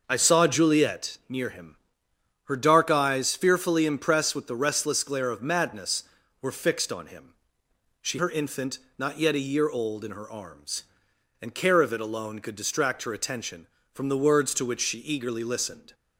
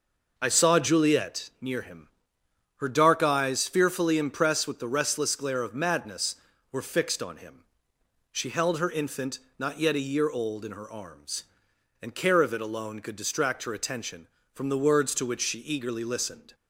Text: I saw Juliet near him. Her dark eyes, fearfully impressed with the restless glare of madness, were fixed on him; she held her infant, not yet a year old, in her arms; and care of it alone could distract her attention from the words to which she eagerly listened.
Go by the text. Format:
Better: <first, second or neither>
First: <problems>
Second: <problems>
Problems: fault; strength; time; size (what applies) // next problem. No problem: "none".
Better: second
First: skips "held"; at 8.1 s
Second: none